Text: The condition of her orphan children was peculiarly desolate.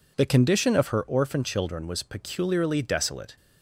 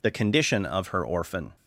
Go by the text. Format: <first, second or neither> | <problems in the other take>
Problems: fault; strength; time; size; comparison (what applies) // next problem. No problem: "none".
first | stops before "children was peculiarly desolate"; at 1.5 s